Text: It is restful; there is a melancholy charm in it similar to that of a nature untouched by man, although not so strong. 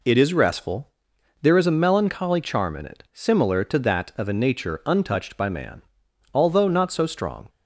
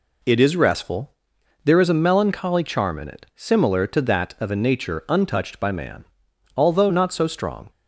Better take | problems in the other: neither | none

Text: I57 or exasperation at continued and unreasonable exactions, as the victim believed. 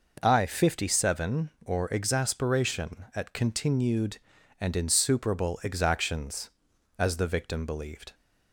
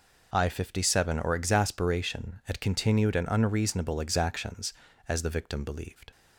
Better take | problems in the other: second | says "insuperable" for "unreasonable"; at 4.7 s

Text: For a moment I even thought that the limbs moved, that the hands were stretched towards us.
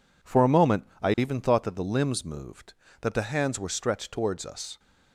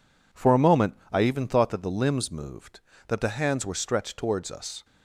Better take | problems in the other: neither | pauses between "moment" and "I"; slight; the same in both

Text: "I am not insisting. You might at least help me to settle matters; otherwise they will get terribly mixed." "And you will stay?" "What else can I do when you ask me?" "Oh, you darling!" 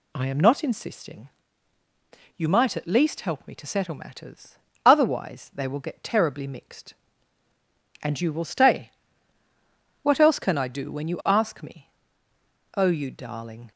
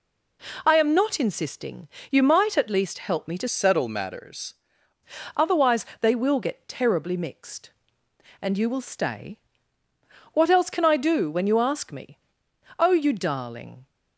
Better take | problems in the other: first | changes voice from "settle" to "matters"; from 3.4 to 4.5 s; 1.1 s long

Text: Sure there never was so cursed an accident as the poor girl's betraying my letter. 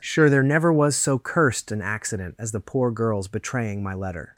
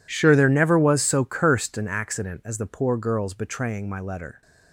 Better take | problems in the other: first | gets quieter; strong; throughout; 20 dB

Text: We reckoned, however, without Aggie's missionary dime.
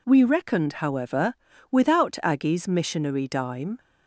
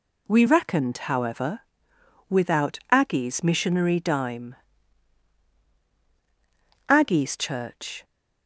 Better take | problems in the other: first | goes on to say "Aggie's church"; noticeable; from 6.8 s on; 1.1 s long

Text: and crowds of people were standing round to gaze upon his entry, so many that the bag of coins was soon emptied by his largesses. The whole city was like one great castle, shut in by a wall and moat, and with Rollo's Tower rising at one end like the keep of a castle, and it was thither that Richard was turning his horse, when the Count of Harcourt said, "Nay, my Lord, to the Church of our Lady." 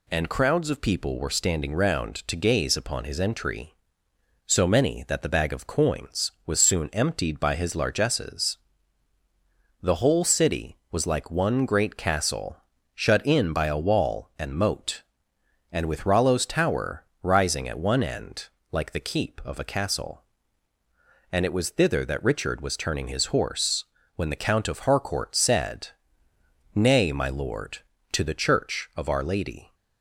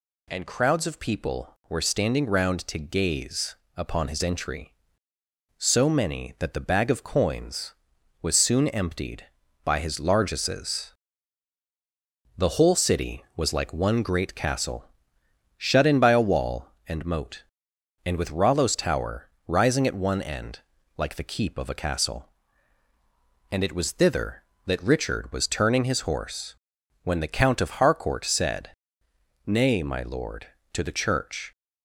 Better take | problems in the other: first | pauses between "gaze" and "upon"; slight; at 3.5 s; 0.22 s long // pauses between "Tower" and "rising"; slight; at 19.2 s; 0.18 s long; slight in the first // pauses between "end" and "like"; slight; at 20.6 s; 0.36 s long; slight in the first // stops before "of our Lady"; at 31.5 s

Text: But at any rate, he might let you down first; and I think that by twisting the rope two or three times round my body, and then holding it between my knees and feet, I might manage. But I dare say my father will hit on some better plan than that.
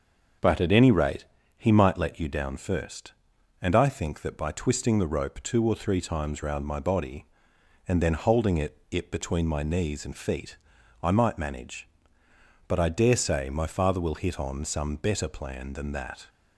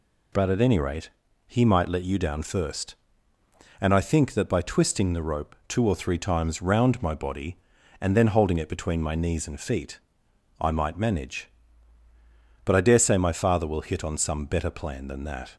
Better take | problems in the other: second | starts louder than the rest; until 1.7 s; 6.5 dB // says "it" twice; at 8.8 s

